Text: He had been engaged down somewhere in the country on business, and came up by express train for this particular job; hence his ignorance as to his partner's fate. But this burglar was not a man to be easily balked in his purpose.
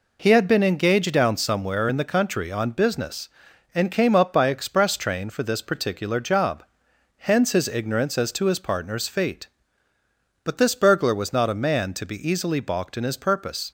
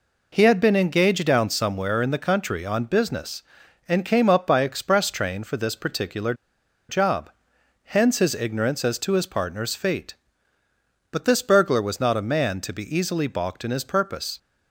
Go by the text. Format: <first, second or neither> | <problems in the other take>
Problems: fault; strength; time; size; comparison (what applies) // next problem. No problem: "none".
first | pauses between "particular" and "job"; noticeable; at 6.3 s; 0.55 s long